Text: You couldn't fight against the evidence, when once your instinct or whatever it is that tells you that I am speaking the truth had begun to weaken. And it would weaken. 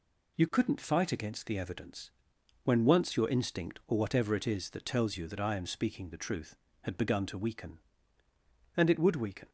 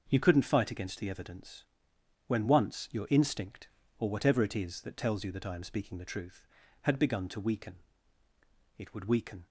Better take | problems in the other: first | skips "And"; at 8.2 s

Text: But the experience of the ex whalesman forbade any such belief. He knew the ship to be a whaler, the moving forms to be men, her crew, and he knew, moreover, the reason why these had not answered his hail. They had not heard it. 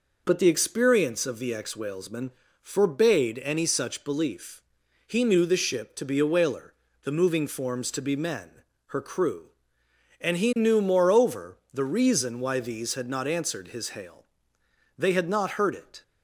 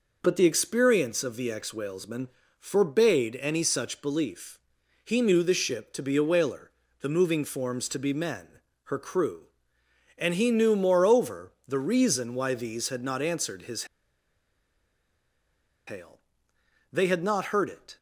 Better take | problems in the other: first | pauses between "whalesman" and "forbade"; slight; at 2.2 s; 0.32 s long; slight in the first // pauses between "his" and "hail"; strong; at 13.8 s; 2.0 s long

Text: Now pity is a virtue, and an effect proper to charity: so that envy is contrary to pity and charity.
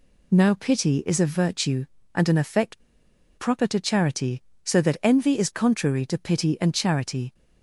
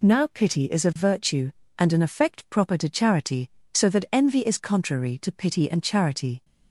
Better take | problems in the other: second | pauses between "effect" and "proper"; noticeable; at 2.8 s; 0.56 s long

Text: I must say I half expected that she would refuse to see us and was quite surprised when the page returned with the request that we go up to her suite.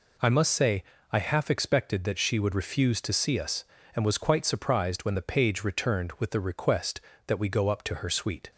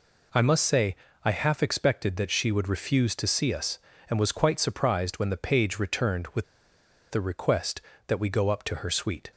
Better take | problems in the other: first | pauses between "say" and "I"; slight; at 0.9 s; 0.28 s long; slight in the first // pauses between "with" and "the"; noticeable; at 6.4 s; 0.66 s long

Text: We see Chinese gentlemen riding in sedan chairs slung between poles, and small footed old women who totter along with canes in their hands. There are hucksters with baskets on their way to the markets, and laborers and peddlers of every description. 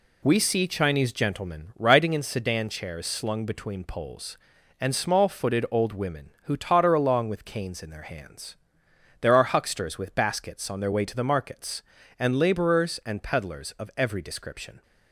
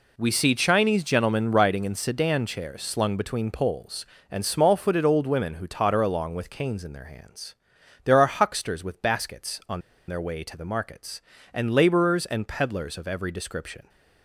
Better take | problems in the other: first | pauses between "on" and "their"; slight; at 9.7 s; 0.28 s long

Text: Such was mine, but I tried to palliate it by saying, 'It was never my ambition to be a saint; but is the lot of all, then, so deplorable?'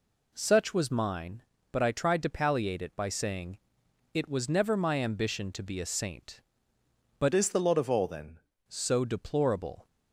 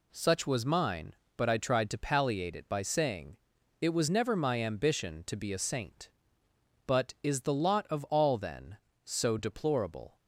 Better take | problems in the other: second | changes voice from "is" to "then"; from 7.3 to 8.3 s; 1.0 s long

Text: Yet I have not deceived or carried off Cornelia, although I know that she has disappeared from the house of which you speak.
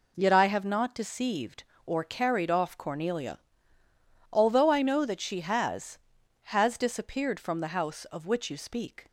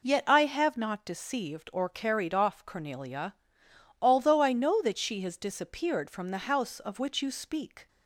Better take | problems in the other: second | says "has" twice; at 6.4 s

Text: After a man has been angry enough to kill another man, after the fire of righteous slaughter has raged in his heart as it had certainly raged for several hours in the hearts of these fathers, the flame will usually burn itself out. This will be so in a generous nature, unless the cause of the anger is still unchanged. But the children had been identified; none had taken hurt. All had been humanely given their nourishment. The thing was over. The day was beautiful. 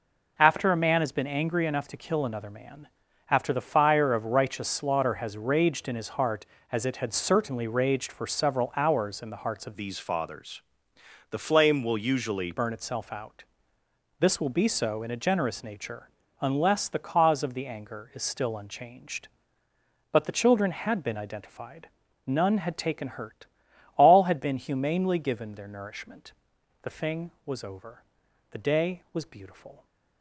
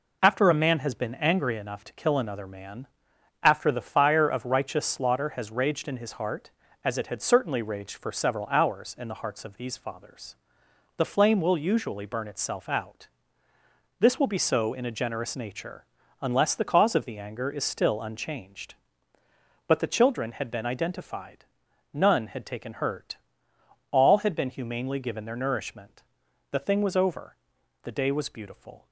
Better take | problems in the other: second | changes voice from "these" to "usually"; from 9.7 to 12.5 s; 2.8 s long

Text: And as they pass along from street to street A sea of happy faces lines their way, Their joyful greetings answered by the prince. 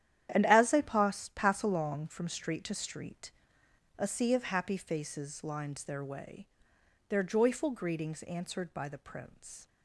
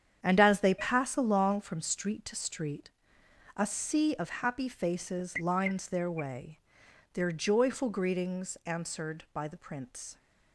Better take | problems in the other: second | starts louder than the rest; strong; until 1.3 s; 10.5 dB; strong in the second // says "pass" twice; at 1.3 s // pauses between "street" and "A"; noticeable; at 3.3 s; 0.66 s long; noticeable in the second

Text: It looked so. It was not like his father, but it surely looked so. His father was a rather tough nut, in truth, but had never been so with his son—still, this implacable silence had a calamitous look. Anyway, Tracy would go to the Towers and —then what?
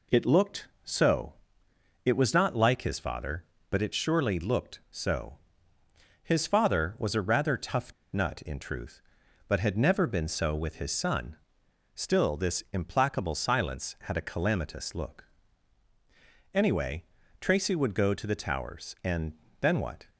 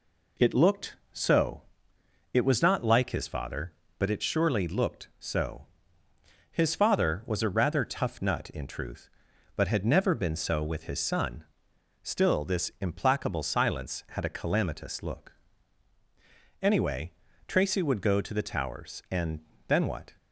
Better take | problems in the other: second | pauses between "tough" and "nut"; slight; at 7.9 s; 0.20 s long

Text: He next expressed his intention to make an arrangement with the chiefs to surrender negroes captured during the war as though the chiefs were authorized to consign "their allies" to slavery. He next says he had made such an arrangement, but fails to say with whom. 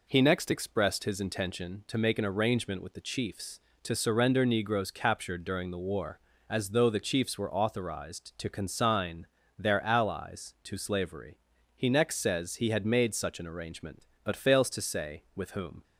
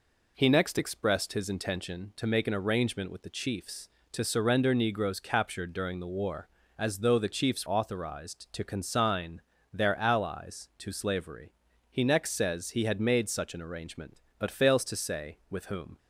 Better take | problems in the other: first | skips "were"; at 7.6 s // pauses between "consign" and "their"; slight; at 9.4 s; 0.32 s long; slight in the first

